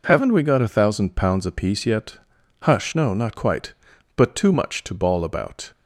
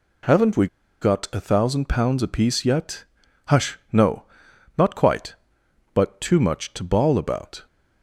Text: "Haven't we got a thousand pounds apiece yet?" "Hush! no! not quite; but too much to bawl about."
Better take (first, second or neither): first